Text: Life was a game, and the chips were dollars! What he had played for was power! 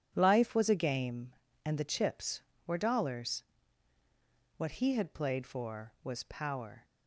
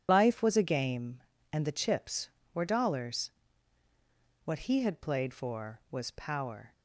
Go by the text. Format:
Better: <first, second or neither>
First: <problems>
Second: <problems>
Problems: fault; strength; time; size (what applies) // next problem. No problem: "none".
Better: first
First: none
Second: loses the start of "Life"; at 0.0 s; 70 ms